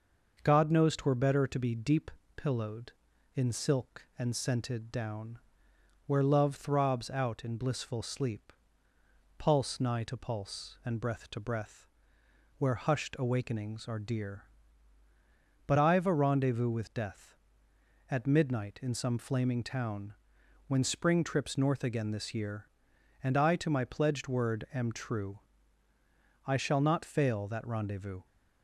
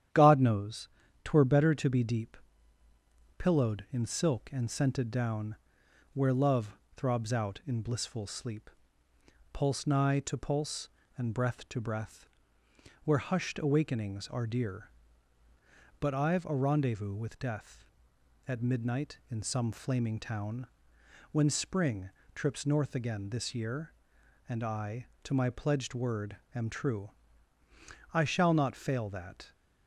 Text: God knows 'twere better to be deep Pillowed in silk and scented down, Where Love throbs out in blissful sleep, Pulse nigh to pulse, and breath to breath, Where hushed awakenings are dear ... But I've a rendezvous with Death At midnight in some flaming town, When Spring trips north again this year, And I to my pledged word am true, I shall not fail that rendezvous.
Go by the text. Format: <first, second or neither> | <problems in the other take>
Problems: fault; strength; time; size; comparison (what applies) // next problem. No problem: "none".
first | starts louder than the rest; strong; until 1.4 s; 10 dB; noticeable in the first // pauses between "knows" and "twere"; slight; at 0.8 s; 0.34 s long // pauses between "deep" and "Pillowed"; at 2.3 s; 1.0 s long; slight in the first // pauses between "Love" and "throbs"; slight; at 6.7 s; 0.20 s long // pauses between "Spring" and "trips"; slight; at 22.0 s; 0.24 s long // pauses between "word" and "am"; slight; at 26.3 s; 0.16 s long // stops before "rendezvous"; at 29.5 s